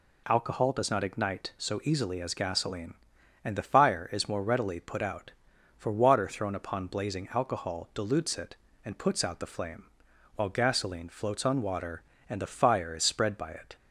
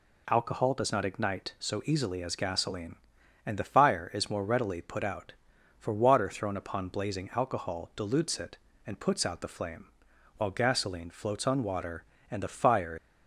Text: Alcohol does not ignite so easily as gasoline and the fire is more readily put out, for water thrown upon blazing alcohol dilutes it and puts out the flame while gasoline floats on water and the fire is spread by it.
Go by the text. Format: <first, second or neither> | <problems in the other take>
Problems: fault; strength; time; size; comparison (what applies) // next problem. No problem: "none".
first | pauses between "flame" and "while"; noticeable; at 9.8 s; 0.50 s long; noticeable in the first // stops before "is spread by it"; at 12.9 s